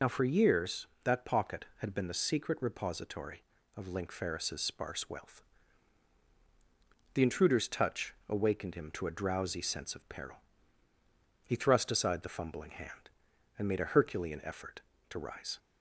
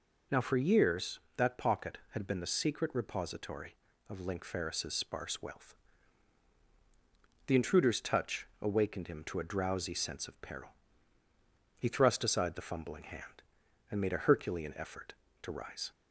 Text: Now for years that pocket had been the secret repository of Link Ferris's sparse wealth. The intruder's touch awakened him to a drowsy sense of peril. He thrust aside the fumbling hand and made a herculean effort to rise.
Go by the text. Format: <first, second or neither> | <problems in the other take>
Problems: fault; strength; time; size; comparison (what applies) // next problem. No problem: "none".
second | loses the start of "Now"; at 0.0 s; 30 ms